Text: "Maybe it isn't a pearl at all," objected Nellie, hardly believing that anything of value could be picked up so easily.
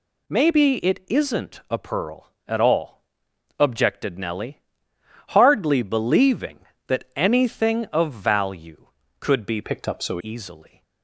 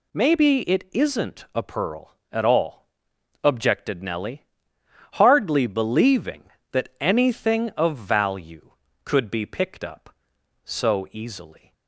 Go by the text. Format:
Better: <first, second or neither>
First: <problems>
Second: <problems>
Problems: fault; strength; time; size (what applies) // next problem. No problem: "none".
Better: second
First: changes voice from "picked" to "so"; from 9.6 to 10.1 s; 0.5 s long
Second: none